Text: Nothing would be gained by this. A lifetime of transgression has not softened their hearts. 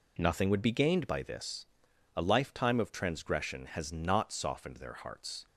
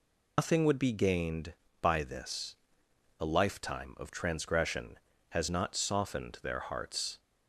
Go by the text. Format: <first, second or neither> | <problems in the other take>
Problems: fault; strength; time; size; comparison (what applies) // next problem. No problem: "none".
first | loses the start of "Nothing"; at 0.3 s; 120 ms